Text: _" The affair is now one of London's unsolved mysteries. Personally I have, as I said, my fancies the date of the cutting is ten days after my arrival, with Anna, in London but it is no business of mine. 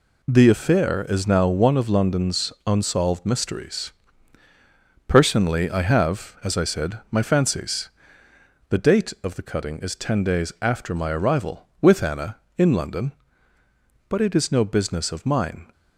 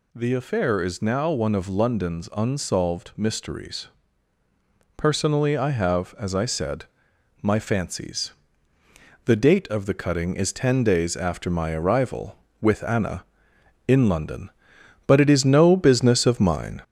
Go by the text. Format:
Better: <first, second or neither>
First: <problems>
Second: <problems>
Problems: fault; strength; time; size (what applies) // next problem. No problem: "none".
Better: first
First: pauses between "fancies" and "the"; noticeable; at 7.8 s; 0.80 s long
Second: gets louder; slight; throughout; 3 dB // pauses between "fancies" and "the"; noticeable; at 8.3 s; 0.94 s long